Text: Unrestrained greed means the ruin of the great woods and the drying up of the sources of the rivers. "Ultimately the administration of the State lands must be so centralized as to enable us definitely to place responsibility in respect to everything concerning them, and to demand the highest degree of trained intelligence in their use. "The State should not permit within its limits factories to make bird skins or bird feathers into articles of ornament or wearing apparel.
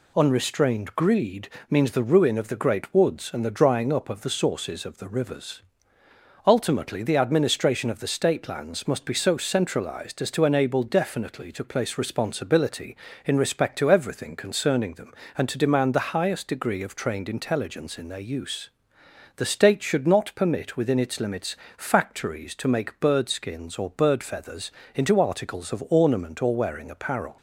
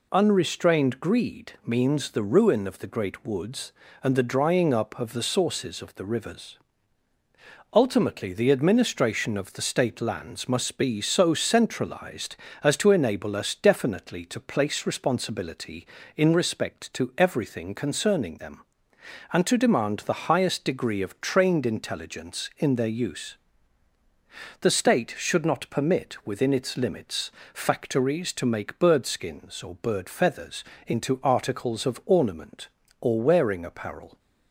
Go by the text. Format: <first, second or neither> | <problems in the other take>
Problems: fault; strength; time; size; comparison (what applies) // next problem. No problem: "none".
second | pauses between "greed" and "means"; slight; at 1.4 s; 0.20 s long // skips "us"; at 10.8 s // pauses between "limits" and "factories"; slight; at 21.5 s; 0.22 s long; slight in the second // pauses between "feathers" and "into"; slight; at 24.7 s; 0.20 s long; slight in the second